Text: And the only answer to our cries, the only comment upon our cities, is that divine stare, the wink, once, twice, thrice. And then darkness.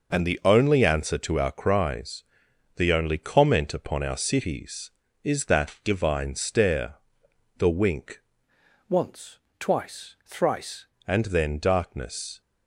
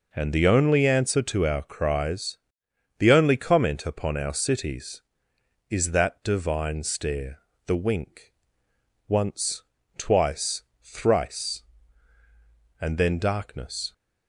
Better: second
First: changes voice from "once" to "thrice"; from 8.8 to 10.8 s; 2.0 s long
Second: none

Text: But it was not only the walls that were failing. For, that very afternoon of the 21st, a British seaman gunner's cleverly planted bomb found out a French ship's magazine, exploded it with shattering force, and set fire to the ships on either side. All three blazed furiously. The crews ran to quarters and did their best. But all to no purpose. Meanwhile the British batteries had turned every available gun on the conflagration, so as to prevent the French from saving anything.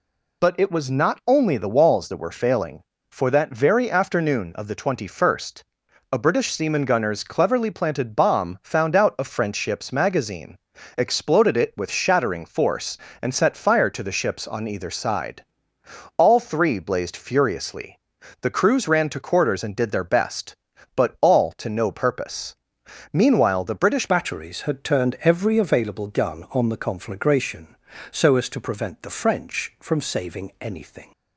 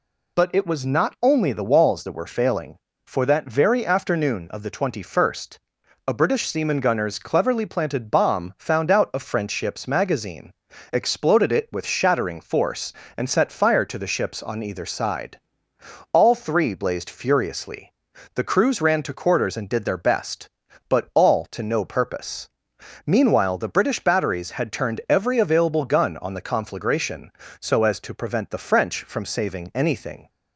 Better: second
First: changes voice at "batteries"; from 24.0 s on; 7.1 s long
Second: none

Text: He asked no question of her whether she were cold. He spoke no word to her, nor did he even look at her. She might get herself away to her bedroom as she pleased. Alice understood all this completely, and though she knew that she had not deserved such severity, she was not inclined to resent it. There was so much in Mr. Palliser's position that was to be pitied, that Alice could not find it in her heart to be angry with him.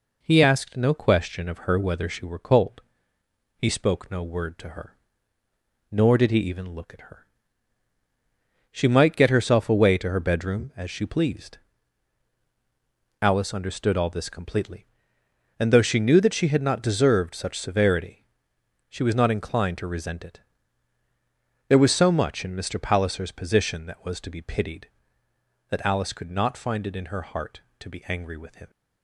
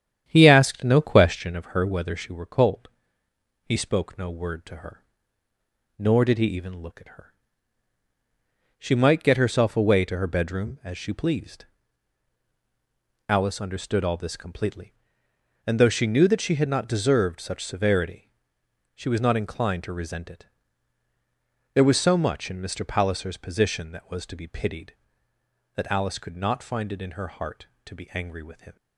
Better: first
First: none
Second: starts louder than the rest; strong; until 1.6 s; 9.5 dB

